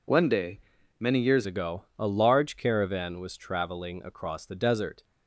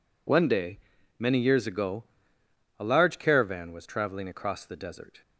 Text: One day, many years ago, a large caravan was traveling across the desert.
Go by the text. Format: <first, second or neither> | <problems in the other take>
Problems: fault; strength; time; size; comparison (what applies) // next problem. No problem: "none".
second | changes voice at "ago"; from 1.4 s on; 3.6 s long